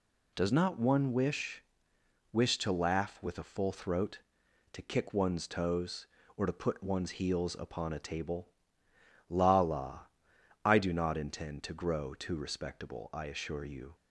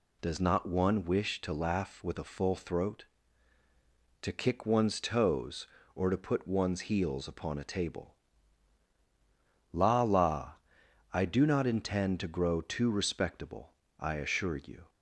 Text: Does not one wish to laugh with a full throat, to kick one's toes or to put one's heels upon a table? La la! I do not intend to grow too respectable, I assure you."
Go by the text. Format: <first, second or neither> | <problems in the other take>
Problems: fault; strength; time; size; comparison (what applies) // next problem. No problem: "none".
second | says "wish" twice; at 2.3 s